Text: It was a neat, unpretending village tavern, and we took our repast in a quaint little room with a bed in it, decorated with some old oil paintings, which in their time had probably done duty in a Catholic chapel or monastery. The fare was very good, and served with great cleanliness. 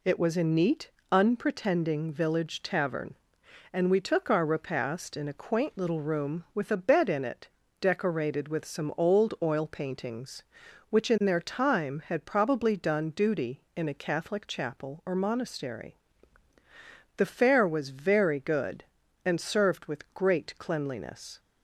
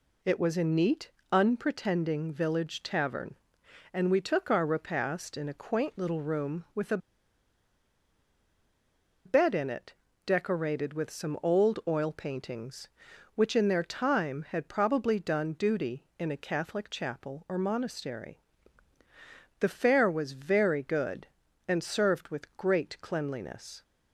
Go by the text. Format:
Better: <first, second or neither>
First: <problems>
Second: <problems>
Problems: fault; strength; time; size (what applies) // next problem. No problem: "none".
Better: first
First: none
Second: pauses between "a" and "bed"; strong; at 6.9 s; 2.2 s long